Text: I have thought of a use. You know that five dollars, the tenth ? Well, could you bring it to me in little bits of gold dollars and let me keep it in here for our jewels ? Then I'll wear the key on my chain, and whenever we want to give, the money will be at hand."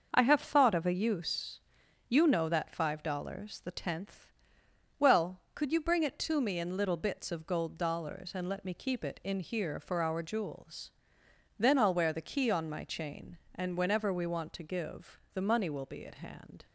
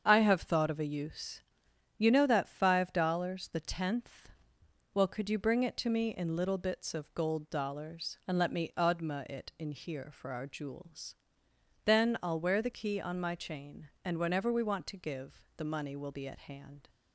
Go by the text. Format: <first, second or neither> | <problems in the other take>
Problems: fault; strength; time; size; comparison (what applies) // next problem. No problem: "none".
first | starts louder than the rest; strong; until 1.0 s; 7 dB; also in the first // says "odma" for "keep"; at 8.7 s